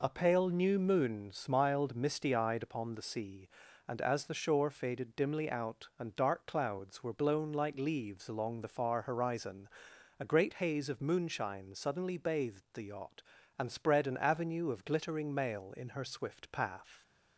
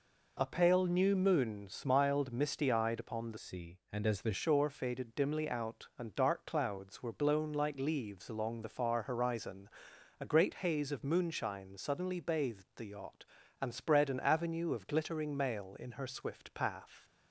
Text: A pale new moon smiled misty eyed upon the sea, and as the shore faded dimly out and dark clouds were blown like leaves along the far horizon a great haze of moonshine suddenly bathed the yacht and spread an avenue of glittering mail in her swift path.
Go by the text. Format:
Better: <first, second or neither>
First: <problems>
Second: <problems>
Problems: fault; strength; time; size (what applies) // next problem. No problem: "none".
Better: first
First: pauses between "horizon" and "a"; noticeable; at 9.6 s; 0.50 s long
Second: changes voice from "sea" to "the"; from 3.3 to 4.3 s; 1.0 s long // pauses between "horizon" and "a"; noticeable; at 9.6 s; 0.50 s long